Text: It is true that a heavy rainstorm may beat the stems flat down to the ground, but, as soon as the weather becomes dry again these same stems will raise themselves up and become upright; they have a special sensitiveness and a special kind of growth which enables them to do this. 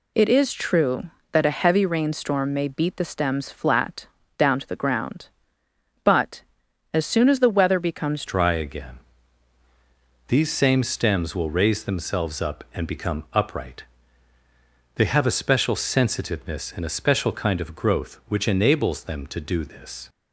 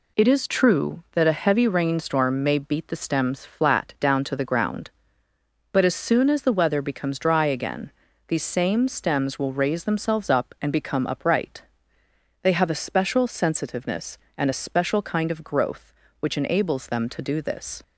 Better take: second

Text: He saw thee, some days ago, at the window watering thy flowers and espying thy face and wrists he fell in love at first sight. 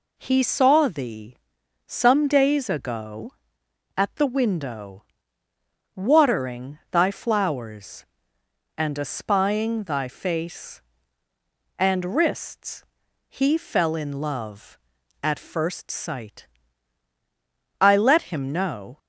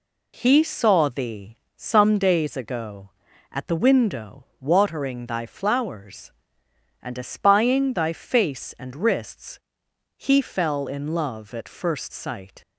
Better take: second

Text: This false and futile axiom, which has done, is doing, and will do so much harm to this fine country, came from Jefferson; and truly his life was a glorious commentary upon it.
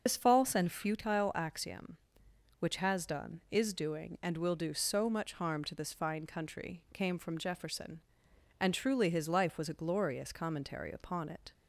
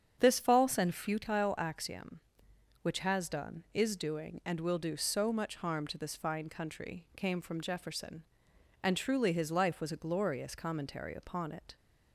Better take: second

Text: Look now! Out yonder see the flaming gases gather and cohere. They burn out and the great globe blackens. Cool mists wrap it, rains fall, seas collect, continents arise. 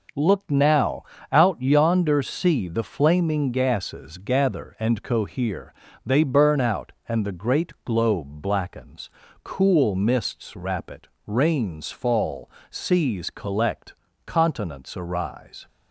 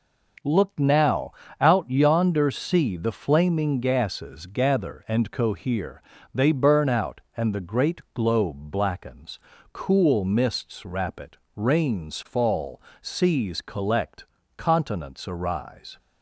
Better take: neither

